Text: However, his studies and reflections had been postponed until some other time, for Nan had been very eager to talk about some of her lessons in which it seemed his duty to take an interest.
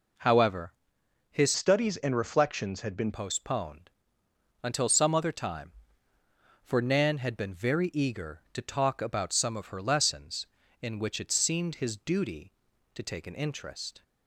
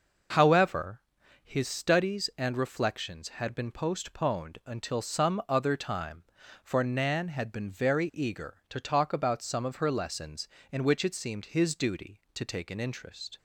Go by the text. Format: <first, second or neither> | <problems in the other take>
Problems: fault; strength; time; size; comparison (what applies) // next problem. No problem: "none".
second | changes voice from "studies" to "been"; from 1.5 to 3.1 s; 1.6 s long // pauses between "postponed" and "until"; noticeable; at 3.8 s; 0.74 s long